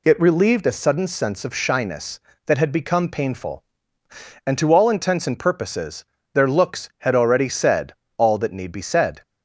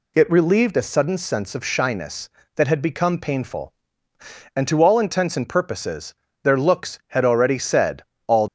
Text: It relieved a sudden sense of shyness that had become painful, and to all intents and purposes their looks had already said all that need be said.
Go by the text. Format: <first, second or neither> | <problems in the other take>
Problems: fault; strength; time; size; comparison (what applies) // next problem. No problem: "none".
first | pauses between "purposes" and "their"; slight; at 6.1 s; 0.30 s long; slight in the first // pauses between "said" and "all"; slight; at 8.0 s; 0.24 s long; slight in the first // stops before "that need be said"; at 8.4 s